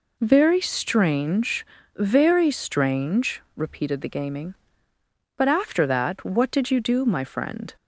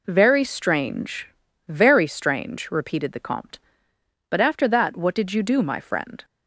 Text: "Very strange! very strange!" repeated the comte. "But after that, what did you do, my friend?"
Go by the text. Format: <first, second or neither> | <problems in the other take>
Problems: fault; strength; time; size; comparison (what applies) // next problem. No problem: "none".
second | says "gaming" for "comte"; at 4.0 s